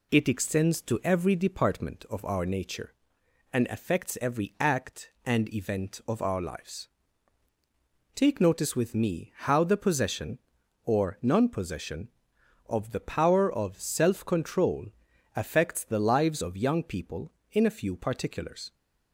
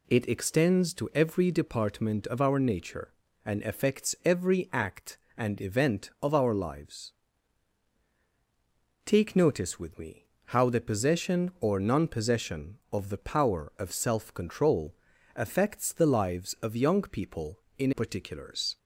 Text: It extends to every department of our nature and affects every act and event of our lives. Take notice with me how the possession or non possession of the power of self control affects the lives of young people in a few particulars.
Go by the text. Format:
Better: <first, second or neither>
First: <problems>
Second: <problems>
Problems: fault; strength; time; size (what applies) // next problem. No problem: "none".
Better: first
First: pauses between "control" and "affects"; noticeable; at 14.8 s; 0.48 s long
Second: pauses between "me" and "how"; slight; at 10.2 s; 0.20 s long // pauses between "control" and "affects"; at 14.9 s; 0.40 s long // skips "a few"; at 17.9 s